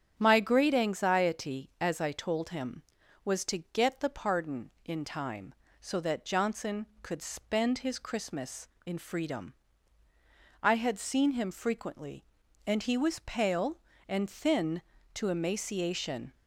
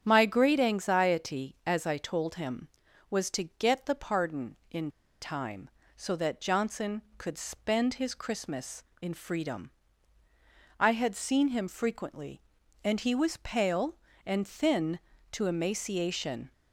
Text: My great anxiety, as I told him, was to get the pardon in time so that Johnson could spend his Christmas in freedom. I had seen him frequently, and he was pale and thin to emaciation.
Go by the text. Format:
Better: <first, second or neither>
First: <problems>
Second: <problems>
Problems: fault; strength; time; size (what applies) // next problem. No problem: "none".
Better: first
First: starts louder than the rest; strong; until 1.1 s; 8 dB // pauses between "to" and "get"; slight; at 3.5 s; 0.16 s long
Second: starts louder than the rest; strong; until 1.0 s; 8.5 dB // pauses between "to" and "get"; slight; at 3.4 s; 0.16 s long // pauses between "in" and "time"; slight; at 4.9 s; 0.31 s long